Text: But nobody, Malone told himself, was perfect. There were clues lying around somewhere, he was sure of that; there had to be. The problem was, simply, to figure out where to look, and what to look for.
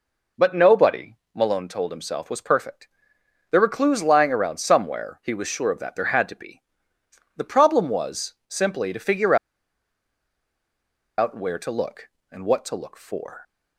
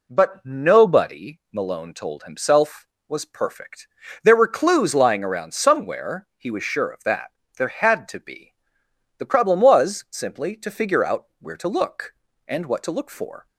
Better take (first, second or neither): second